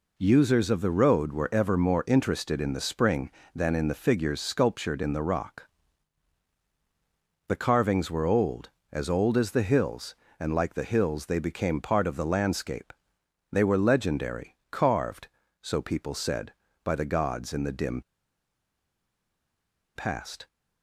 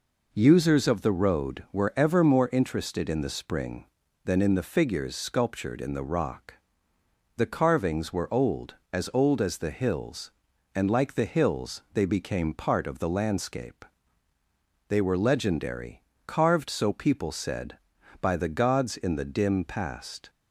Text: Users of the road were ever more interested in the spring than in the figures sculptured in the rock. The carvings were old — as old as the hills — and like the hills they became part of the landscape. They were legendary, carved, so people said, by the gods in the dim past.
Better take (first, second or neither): second